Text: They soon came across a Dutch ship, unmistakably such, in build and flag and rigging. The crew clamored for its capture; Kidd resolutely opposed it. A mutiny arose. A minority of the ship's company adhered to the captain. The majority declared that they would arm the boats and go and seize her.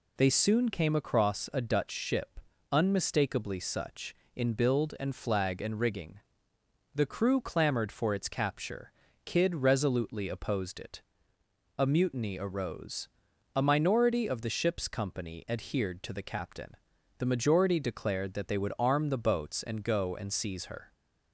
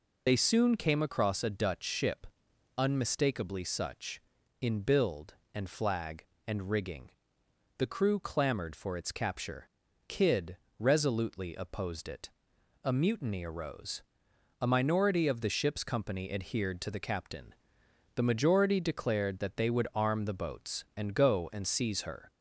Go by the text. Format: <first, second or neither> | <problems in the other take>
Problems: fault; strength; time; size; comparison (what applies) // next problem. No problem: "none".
first | loses the start of "They"; at 0.2 s; 40 ms // pauses between "Kidd" and "resolutely"; slight; at 10.5 s; 0.22 s long